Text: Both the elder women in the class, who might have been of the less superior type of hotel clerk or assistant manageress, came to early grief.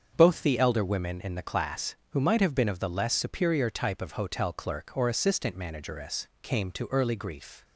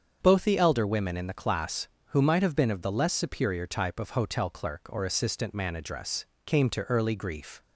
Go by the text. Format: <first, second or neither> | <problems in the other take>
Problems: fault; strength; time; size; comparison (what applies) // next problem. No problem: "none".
neither | starts louder than the rest; the same in both